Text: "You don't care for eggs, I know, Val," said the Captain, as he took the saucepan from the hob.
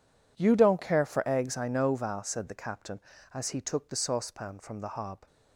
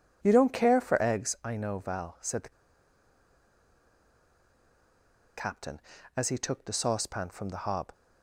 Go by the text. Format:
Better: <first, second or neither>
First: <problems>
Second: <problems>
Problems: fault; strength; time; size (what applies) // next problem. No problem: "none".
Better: first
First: none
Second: pauses between "the" and "Captain"; strong; at 2.5 s; 2.8 s long